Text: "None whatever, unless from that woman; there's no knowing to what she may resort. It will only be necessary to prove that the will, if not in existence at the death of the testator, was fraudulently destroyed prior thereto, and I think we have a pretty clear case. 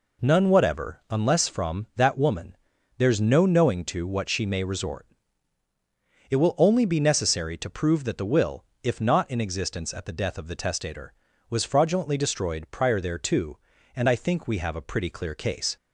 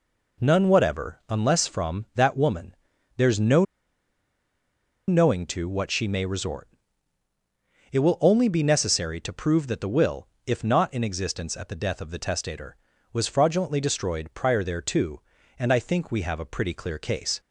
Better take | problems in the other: first | pauses between "no" and "knowing"; strong; at 3.6 s; 1.4 s long

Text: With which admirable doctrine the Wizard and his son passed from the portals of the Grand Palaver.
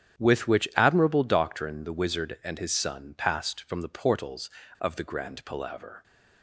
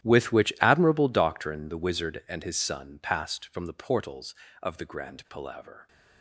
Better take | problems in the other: first | gets quieter; strong; throughout; 18.5 dB // starts louder than the rest; strong; until 1.1 s; 13 dB; strong in the first

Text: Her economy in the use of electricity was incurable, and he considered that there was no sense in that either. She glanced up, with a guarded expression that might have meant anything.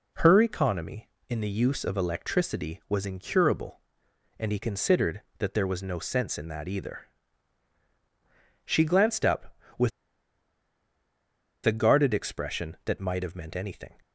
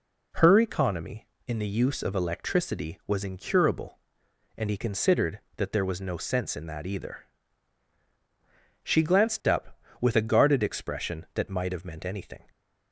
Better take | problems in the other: second | pauses between "with" and "a"; strong; at 9.9 s; 1.7 s long

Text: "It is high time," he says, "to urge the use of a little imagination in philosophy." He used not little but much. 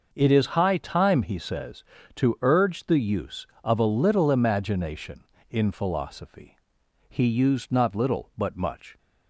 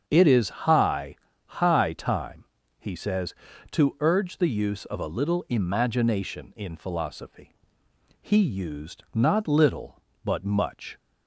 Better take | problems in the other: first | starts louder than the rest; strong; until 1.0 s; 7 dB // says "high" twice; at 1.4 s

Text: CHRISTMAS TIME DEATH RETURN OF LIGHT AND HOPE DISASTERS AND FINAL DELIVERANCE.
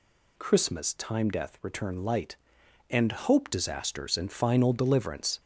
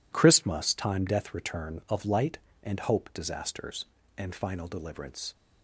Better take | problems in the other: second | skips "OF"; at 2.0 s

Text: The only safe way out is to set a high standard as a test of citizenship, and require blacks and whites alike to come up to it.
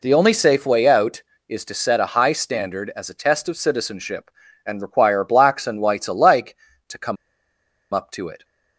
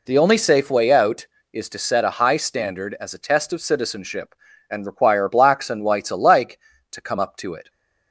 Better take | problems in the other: second | pauses between "come" and "up"; noticeable; at 7.1 s; 0.77 s long

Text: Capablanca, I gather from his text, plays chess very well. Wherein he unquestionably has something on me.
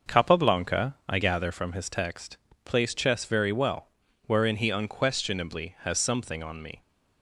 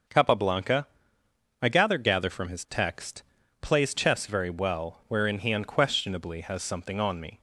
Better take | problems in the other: first | starts louder than the rest; until 1.8 s; 6.5 dB; noticeable in the first // says "gather" twice; at 1.9 s

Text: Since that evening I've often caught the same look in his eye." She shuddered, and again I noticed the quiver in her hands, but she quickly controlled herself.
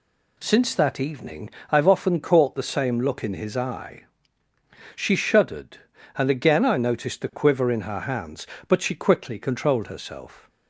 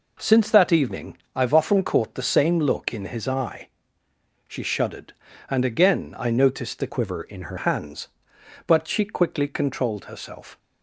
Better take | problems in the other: first | pauses between "evening" and "I've"; slight; at 1.1 s; 0.18 s long; slight in the first // changes voice from "quiver" to "her"; from 6.8 to 7.5 s; 0.7 s long

